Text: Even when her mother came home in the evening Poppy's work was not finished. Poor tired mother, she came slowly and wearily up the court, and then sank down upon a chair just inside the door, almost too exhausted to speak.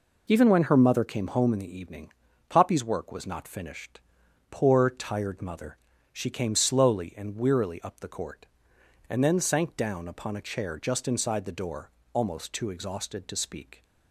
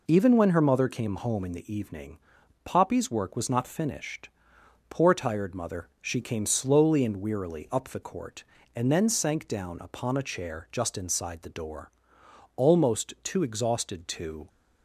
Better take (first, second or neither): first